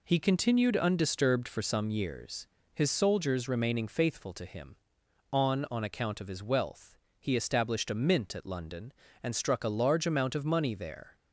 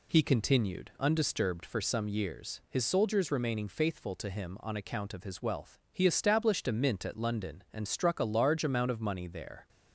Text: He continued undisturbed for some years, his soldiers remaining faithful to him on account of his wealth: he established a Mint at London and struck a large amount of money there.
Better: second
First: says "on" twice; at 5.7 s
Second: none

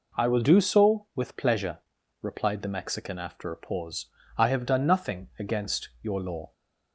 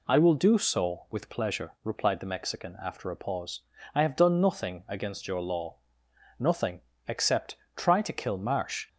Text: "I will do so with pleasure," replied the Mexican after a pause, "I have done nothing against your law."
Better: first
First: none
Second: goes on to say "Nothing except try to kill Marsh"; strong; from 6.3 s on; 2.5 s long

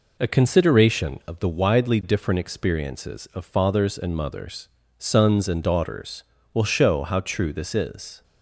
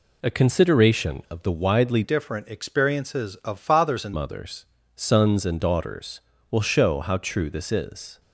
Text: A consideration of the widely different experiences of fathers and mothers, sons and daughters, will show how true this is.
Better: first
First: none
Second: changes voice from "different" to "and"; from 2.0 to 4.1 s; 2.1 s long

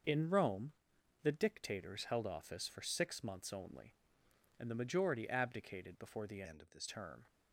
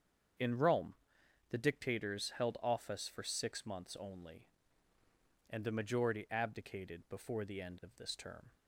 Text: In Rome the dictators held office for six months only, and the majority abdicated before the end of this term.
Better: second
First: starts louder than the rest; until 1.5 s; 6 dB // pauses between "Rome" and "the"; noticeable; at 0.7 s; 0.50 s long // changes voice from "end" to "this"; from 6.4 to 6.8 s; 0.4 s long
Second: starts louder than the rest; strong; until 1.9 s; 7.5 dB // pauses between "Rome" and "the"; noticeable; at 0.9 s; 0.56 s long

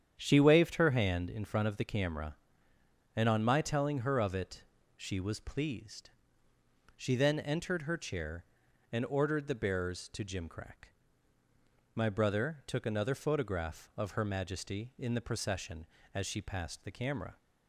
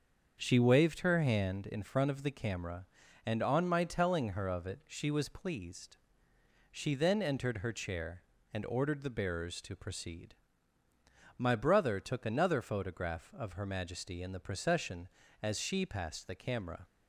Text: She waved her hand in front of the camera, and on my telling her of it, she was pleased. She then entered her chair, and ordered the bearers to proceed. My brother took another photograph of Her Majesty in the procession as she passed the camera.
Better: second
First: starts louder than the rest; strong; until 1.2 s; 8.5 dB // says "jimcrack" for "proceed"; at 10.2 s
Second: starts louder than the rest; until 1.4 s; 7 dB

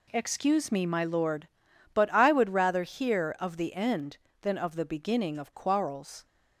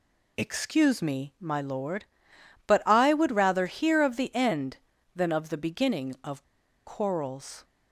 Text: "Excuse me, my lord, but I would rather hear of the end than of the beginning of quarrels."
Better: first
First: none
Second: pauses between "of" and "quarrels"; at 6.4 s; 0.44 s long

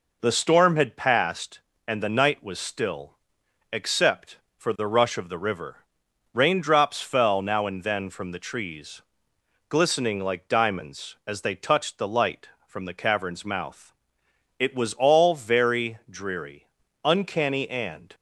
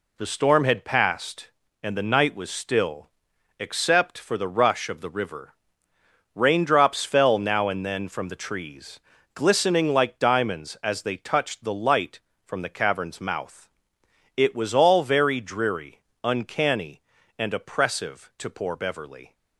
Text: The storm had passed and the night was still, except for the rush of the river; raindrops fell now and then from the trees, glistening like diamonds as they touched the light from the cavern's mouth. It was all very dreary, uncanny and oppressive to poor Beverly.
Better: second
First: stops before "oppressive to poor Beverly"; at 18.1 s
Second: none

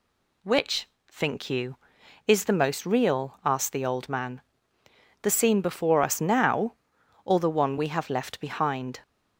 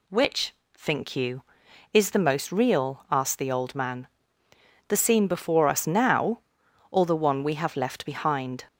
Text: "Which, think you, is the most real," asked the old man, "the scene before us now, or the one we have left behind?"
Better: neither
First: none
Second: none

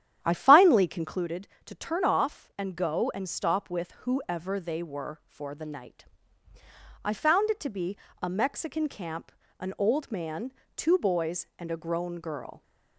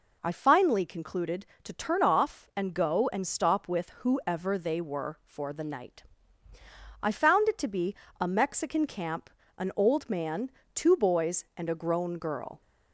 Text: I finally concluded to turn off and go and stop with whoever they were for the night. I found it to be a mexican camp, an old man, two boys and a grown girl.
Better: second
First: starts louder than the rest; strong; until 1.3 s; 10 dB // pauses between "be" and "a"; slight; at 7.9 s; 0.24 s long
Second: pauses between "be" and "a"; slight; at 7.9 s; 0.24 s long

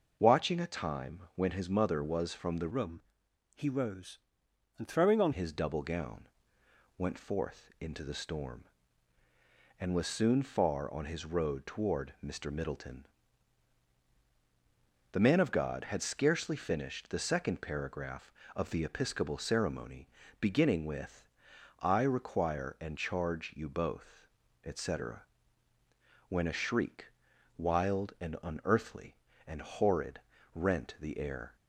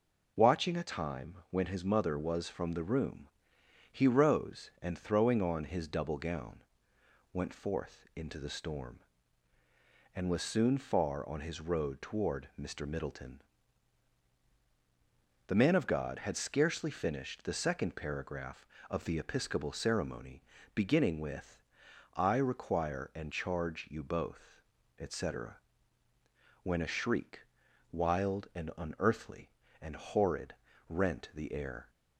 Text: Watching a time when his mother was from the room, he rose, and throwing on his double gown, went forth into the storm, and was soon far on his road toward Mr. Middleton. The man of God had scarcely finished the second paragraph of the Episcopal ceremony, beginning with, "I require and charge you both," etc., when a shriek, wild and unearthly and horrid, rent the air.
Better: second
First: starts louder than the rest; noticeable; until 1.2 s; 6 dB // changes voice from "room" to "on"; from 2.6 to 5.3 s; 2.7 s long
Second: none

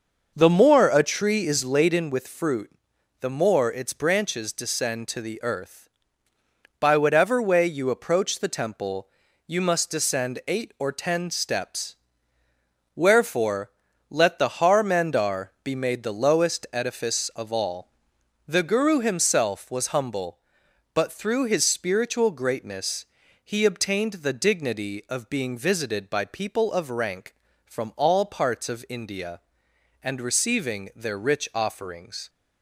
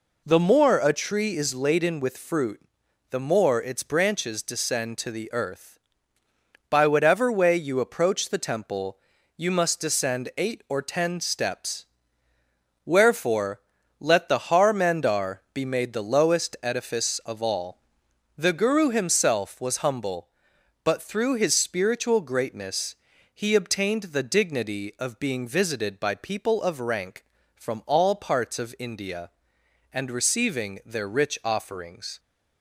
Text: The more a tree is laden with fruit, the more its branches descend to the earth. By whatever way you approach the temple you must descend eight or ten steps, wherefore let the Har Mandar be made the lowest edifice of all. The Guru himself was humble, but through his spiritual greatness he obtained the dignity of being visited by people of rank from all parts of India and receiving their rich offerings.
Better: second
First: starts louder than the rest; noticeable; until 2.1 s; 6 dB // pauses between "temple" and "you"; slight; at 9.0 s; 0.36 s long // pauses between "wherefore" and "let"; at 13.6 s; 0.40 s long // pauses between "greatness" and "he"; at 23.0 s; 0.40 s long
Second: pauses between "temple" and "you"; slight; at 8.9 s; 0.36 s long // pauses between "wherefore" and "let"; at 13.5 s; 0.40 s long // pauses between "greatness" and "he"; at 22.9 s; 0.40 s long

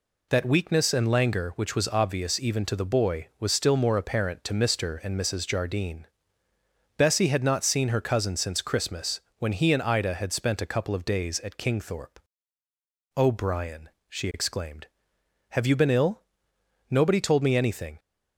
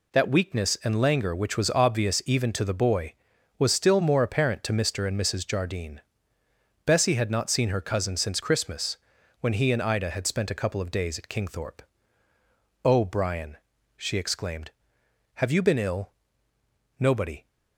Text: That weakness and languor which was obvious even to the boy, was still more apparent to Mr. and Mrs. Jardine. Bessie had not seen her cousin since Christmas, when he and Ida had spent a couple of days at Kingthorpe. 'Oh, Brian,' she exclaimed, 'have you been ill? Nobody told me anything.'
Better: first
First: none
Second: stops before "told me anything"; at 17.4 s

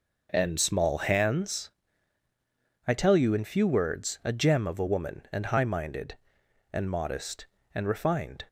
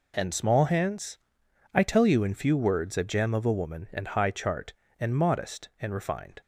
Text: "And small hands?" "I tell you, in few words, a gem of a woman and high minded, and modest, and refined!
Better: first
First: none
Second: says "chart" for "minded"; at 4.3 s

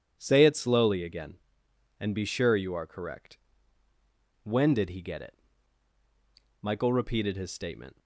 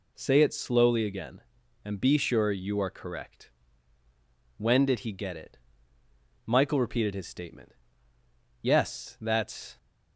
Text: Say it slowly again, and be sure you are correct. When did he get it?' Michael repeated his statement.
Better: first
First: none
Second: goes on to say "Yes that's"; noticeable; from 8.6 s on; 1.1 s long

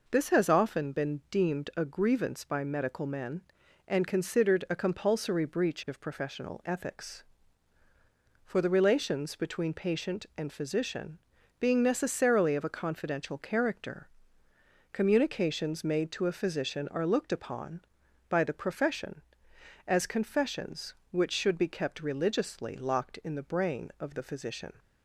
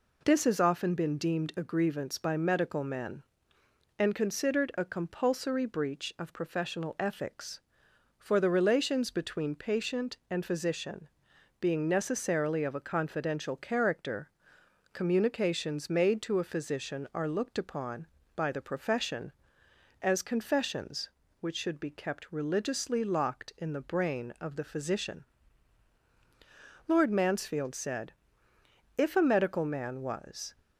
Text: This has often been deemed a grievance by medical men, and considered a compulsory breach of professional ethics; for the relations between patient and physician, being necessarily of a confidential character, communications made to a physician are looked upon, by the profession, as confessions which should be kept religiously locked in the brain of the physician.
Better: first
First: none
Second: goes on to say "Lord Mansfield said If a medical man was"; strong; from 26.8 s on; 3.6 s long

